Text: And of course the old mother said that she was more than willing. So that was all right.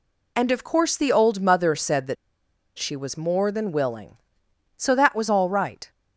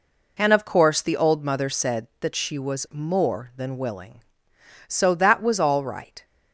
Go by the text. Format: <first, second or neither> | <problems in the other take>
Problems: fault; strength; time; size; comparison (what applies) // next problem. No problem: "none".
second | pauses between "that" and "she"; noticeable; at 2.1 s; 0.62 s long